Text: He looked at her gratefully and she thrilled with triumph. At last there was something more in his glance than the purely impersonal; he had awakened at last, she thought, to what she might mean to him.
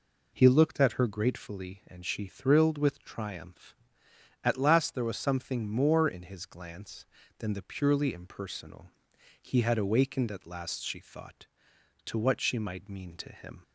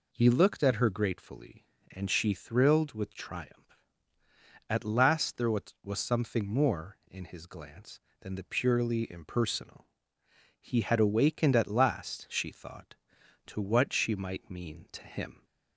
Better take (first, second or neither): first